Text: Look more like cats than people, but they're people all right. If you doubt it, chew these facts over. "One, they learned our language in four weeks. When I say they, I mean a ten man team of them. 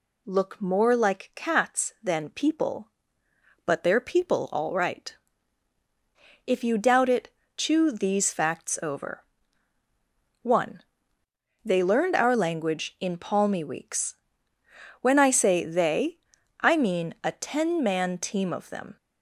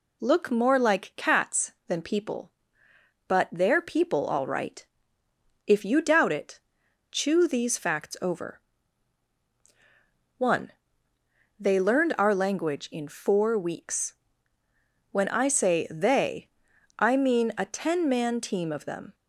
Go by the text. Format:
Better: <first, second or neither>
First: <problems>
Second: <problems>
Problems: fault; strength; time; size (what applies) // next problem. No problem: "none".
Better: second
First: says "palmy" for "four"; at 13.1 s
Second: none